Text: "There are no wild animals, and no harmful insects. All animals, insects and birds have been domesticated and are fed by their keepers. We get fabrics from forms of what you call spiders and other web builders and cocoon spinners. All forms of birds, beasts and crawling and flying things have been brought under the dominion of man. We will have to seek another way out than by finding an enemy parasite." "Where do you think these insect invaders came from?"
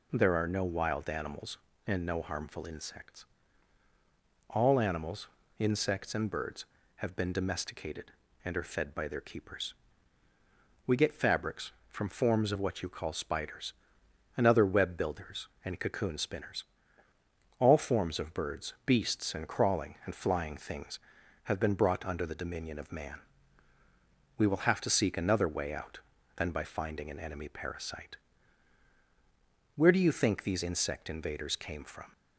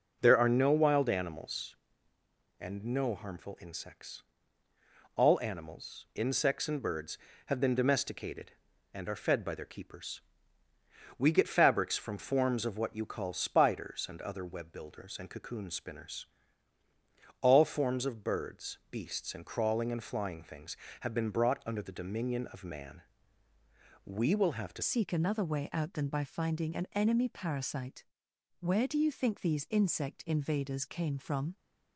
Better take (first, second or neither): first